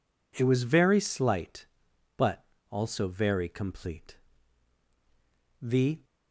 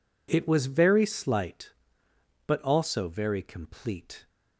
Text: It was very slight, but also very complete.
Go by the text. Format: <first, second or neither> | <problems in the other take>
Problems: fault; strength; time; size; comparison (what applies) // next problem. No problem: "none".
second | pauses between "but" and "also"; slight; at 2.4 s; 0.28 s long // goes on to say "The"; slight; from 5.6 s on; 0.42 s long